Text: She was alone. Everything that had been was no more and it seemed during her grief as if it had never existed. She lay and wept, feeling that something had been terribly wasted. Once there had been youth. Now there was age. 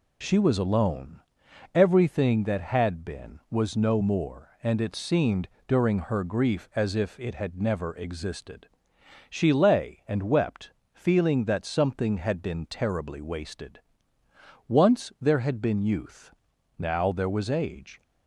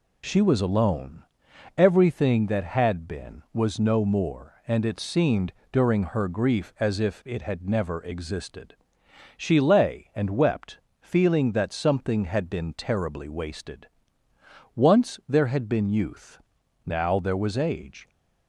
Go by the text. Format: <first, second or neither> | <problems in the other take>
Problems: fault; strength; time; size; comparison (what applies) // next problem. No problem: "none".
neither | pauses between "seemed" and "during"; slight; the same in both